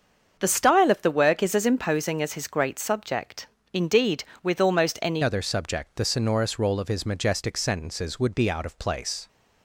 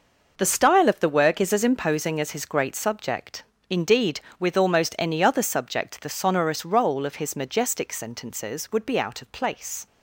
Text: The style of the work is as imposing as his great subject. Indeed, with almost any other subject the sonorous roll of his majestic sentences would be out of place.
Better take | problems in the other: second | starts louder than the rest; until 1.4 s; 7 dB // changes voice at "other"; from 5.2 s on; 4.0 s long

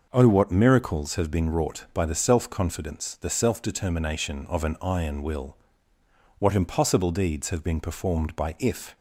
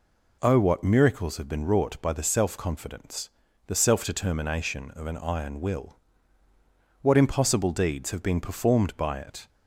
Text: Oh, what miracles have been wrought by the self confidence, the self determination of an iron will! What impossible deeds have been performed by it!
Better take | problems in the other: second | says "if" for "it"; at 8.5 s

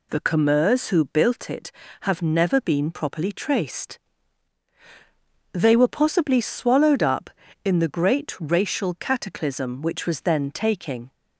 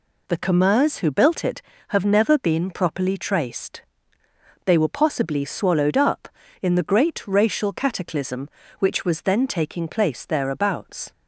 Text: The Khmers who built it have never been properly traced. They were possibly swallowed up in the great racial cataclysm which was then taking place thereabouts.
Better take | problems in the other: second | stops before "place thereabouts"; at 11.1 s

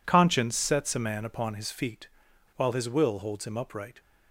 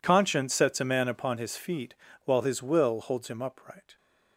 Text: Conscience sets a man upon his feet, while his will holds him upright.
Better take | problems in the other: neither | none

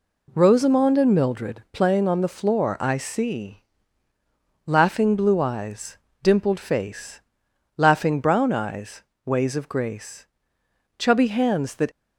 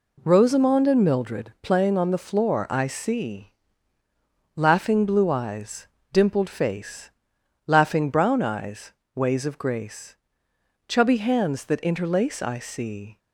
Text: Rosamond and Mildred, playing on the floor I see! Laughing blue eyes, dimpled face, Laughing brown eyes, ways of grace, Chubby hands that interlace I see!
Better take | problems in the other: second | stops before "interlace I see"; at 11.9 s

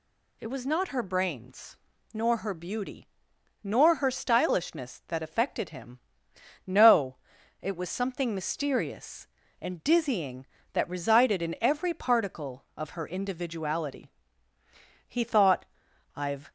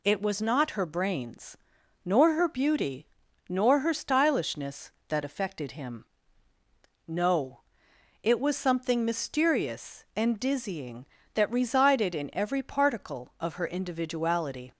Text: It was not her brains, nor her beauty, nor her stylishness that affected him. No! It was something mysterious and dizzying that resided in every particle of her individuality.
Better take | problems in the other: second | goes on to say "He thought I've"; from 15.0 s on; 1.4 s long

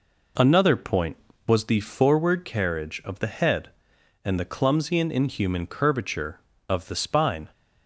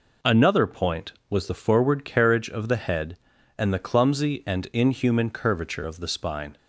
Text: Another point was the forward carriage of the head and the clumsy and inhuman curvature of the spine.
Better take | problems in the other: neither | none

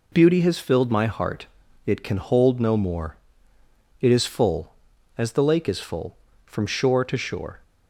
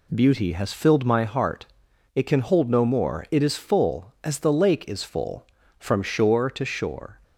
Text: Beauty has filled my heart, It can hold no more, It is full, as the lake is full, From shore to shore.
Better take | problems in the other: neither | none

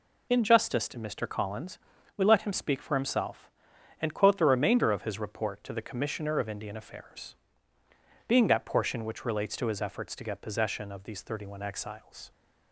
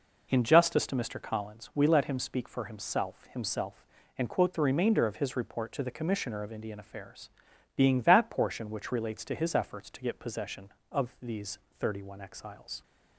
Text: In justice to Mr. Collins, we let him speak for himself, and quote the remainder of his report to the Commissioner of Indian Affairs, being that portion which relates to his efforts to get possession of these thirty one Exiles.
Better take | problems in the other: first | says "himself" twice; at 3.3 s // pauses between "these" and "thirty"; slight; at 11.5 s; 0.22 s long

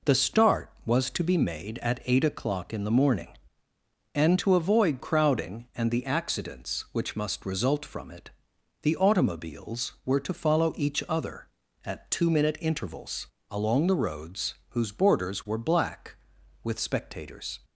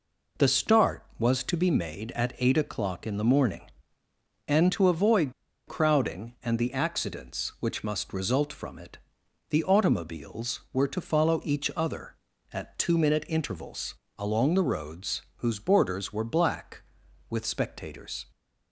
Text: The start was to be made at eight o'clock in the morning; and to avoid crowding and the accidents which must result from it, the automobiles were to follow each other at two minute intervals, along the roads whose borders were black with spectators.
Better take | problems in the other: first | pauses between "avoid" and "crowding"; slight; at 5.3 s; 0.35 s long // pauses between "roads" and "whose"; slight; at 15.2 s; 0.16 s long; slight in the first

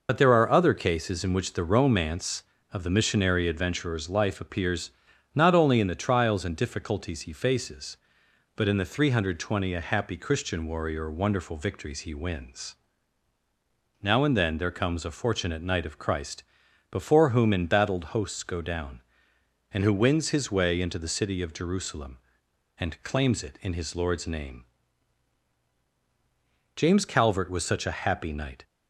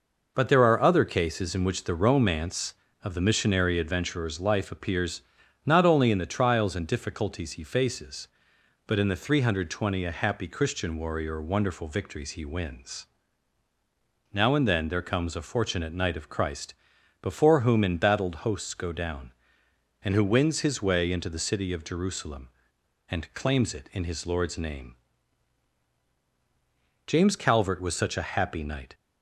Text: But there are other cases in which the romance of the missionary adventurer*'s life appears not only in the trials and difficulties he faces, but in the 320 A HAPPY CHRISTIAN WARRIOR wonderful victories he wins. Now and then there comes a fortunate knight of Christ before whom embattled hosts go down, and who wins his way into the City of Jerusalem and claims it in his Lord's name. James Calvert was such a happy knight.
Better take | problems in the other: second | loses the start of "But"; at 0.0 s; 60 ms // pauses between "appears" and "not"; at 4.9 s; 0.44 s long; also in the second // pauses between "Christ" and "before"; noticeable; at 16.4 s; 0.48 s long; noticeable in the second

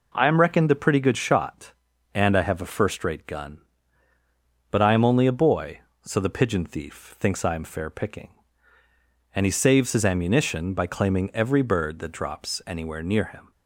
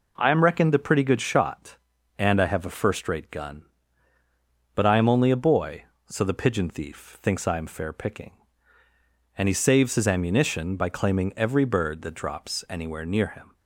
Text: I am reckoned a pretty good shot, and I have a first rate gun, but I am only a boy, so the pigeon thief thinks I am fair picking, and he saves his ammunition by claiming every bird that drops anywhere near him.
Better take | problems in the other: neither | none

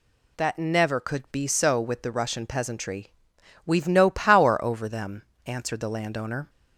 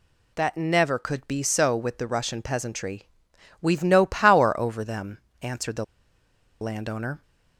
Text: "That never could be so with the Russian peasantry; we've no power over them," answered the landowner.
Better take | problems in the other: first | pauses between "the" and "landowner"; noticeable; at 5.8 s; 0.76 s long

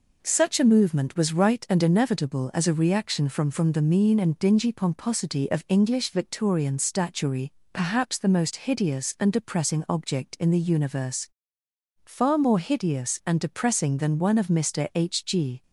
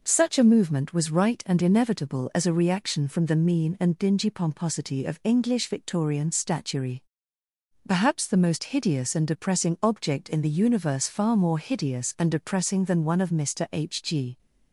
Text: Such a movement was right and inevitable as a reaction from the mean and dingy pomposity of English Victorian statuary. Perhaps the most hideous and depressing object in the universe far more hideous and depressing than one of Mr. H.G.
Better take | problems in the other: second | says "from" twice; at 3.5 s // pauses between "universe" and "far"; noticeable; at 11.2 s; 0.76 s long

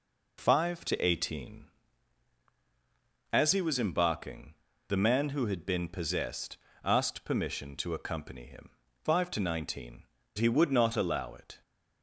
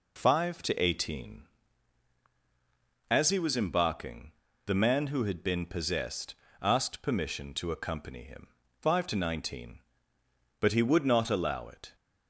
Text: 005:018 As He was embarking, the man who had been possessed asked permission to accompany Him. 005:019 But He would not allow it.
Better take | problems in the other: second | pauses between "possessed" and "asked"; slight; at 6.5 s; 0.26 s long; slight in the second // skips "But"; at 10.2 s

